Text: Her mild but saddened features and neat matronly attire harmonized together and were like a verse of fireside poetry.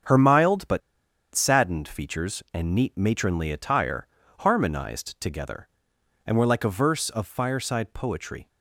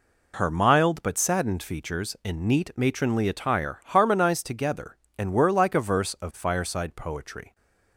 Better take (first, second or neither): second